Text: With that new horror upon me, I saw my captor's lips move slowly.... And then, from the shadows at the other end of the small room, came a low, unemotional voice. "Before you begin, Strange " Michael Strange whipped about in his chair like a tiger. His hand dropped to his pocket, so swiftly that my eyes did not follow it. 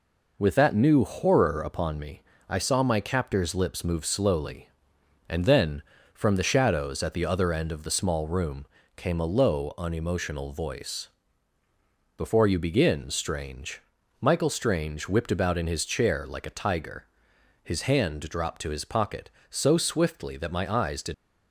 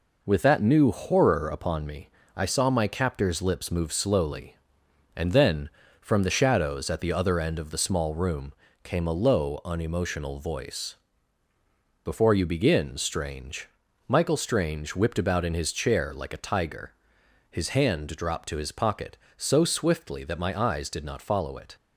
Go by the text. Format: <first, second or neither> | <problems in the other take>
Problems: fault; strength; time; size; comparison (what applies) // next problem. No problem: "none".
second | stops before "not follow it"; at 21.1 s